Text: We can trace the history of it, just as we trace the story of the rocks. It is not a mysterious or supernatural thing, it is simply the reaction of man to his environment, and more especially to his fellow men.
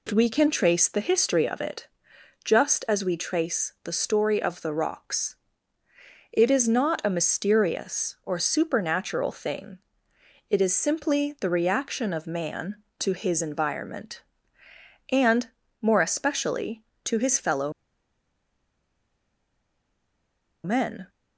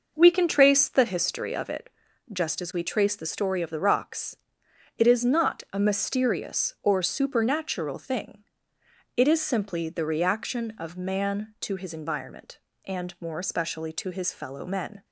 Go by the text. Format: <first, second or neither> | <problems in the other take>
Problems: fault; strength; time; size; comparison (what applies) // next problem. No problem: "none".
second | pauses between "and" and "more"; slight; at 15.4 s; 0.32 s long // pauses between "fellow" and "men"; strong; at 17.7 s; 2.9 s long